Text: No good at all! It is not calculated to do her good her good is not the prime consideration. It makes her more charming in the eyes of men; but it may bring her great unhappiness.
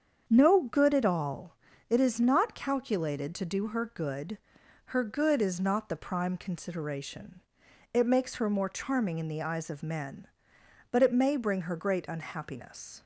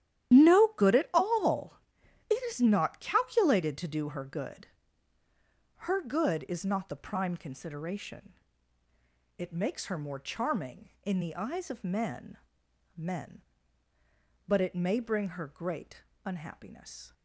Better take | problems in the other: first | starts louder than the rest; strong; until 1.4 s; 11.5 dB; strong in the first // pauses between "good" and "her"; at 4.6 s; 1.1 s long; noticeable in the first // says "men" twice; at 12.9 s // pauses between "great" and "unhappiness"; slight; at 16.0 s; 0.24 s long

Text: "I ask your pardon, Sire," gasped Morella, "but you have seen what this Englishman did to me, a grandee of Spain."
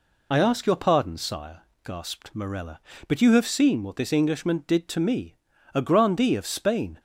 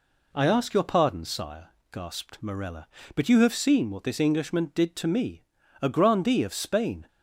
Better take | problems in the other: second | loses the start of "I"; at 0.3 s; 50 ms

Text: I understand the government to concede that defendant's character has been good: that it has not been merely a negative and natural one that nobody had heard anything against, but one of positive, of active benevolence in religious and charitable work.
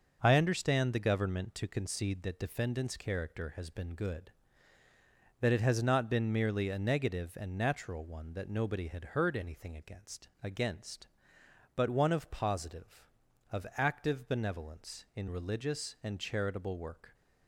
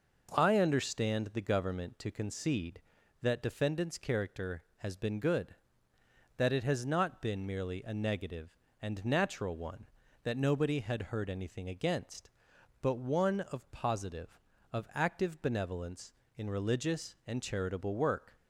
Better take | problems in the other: second | says "against" twice; at 10.4 s

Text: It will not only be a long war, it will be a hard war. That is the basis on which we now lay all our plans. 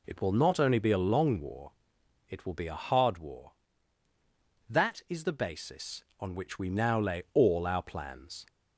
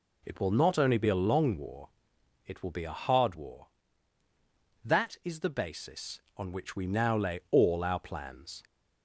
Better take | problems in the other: neither | none

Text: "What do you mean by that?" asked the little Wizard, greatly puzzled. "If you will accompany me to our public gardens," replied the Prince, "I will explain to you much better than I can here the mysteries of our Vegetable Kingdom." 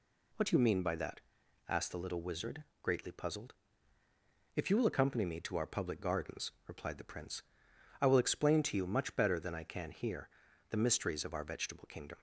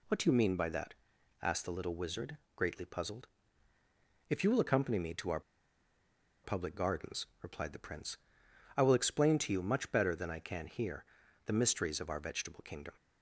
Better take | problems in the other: first | pauses between "our" and "public"; at 5.4 s; 1.0 s long // pauses between "here" and "the"; at 11.0 s; 0.40 s long; also in the first

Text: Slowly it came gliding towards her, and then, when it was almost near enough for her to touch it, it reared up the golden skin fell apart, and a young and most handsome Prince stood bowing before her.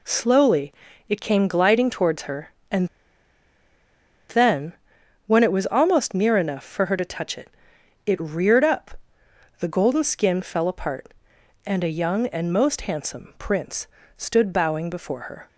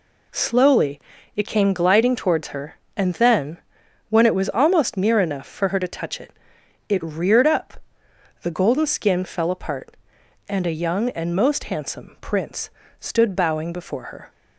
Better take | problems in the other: second | pauses between "Slowly" and "it"; slight; at 0.7 s; 0.36 s long; slight in the second // pauses between "and" and "then"; strong; at 2.8 s; 1.4 s long // pauses between "up" and "the"; noticeable; at 8.9 s; 0.64 s long; noticeable in the second // pauses between "Prince" and "stood"; slight; at 13.8 s; 0.32 s long; slight in the second

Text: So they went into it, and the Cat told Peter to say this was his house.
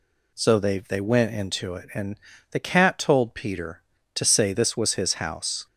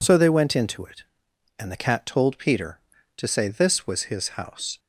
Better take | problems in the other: second | says "they" twice; at 0.7 s // pauses between "and" and "the"; slight; at 2.1 s; 0.34 s long

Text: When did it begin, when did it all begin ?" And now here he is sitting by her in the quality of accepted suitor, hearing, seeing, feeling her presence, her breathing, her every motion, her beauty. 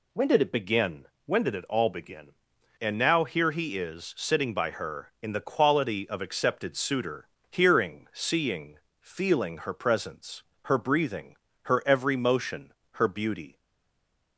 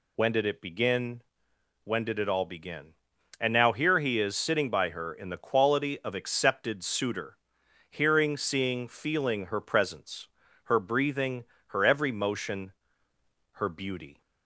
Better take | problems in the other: second | stays silent after the last word; slight; from 13.5 s on; 0.8 s long

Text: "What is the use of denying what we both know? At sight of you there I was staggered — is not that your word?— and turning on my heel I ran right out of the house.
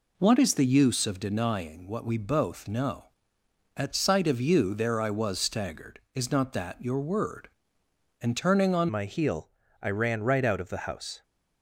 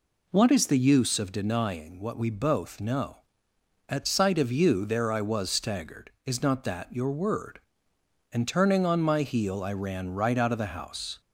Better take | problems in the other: second | changes voice at "my"; from 8.9 s on; 2.3 s long // pauses between "heel" and "I"; slight; at 9.5 s; 0.30 s long

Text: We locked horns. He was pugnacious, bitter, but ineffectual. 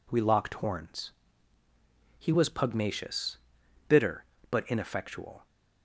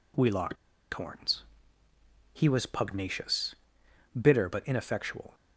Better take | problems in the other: first | pauses between "locked" and "horns"; at 0.5 s; 0.38 s long

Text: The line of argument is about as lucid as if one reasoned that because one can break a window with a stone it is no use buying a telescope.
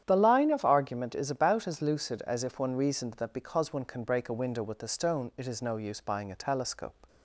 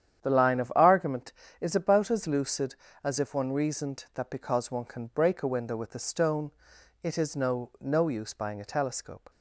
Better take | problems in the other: first | starts louder than the rest; strong; until 1.2 s; 9.5 dB; strong in the first // pauses between "stone" and "it"; noticeable; at 6.4 s; 0.52 s long // says "no" twice; at 7.7 s

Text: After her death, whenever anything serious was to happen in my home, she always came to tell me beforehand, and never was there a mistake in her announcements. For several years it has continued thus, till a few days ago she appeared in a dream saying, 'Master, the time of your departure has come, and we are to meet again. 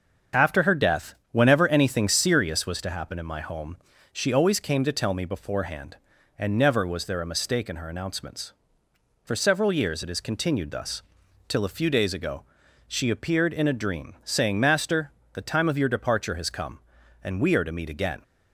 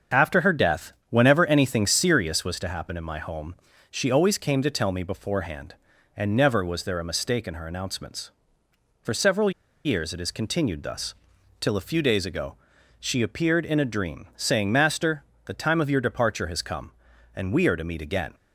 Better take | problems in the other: first | starts louder than the rest; until 1.2 s; 6.5 dB; also in the first // pauses between "several" and "years"; slight; at 9.5 s; 0.34 s long // pauses between "ago" and "she"; at 12.5 s; 0.44 s long; also in the first

